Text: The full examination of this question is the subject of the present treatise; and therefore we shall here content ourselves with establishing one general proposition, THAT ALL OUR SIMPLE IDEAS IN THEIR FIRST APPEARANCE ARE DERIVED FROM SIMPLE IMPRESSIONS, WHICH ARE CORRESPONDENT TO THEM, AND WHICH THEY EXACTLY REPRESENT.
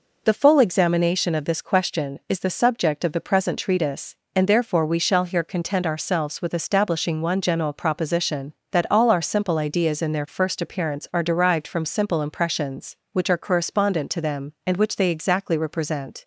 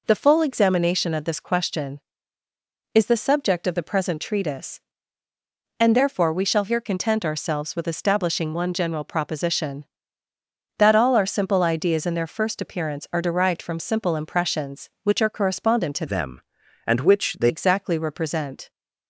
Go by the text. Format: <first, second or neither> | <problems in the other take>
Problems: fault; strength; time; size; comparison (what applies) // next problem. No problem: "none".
first | changes voice from "THEM" to "THEY"; from 16.0 to 17.5 s; 1.5 s long